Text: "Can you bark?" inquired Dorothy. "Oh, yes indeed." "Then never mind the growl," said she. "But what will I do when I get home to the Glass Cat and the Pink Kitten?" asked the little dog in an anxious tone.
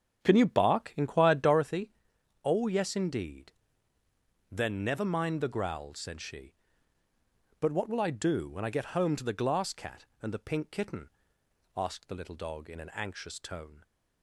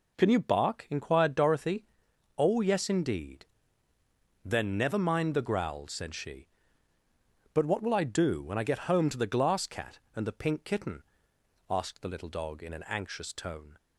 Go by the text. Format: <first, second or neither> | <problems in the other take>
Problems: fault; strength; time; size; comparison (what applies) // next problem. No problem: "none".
second | starts louder than the rest; strong; until 1.8 s; 8 dB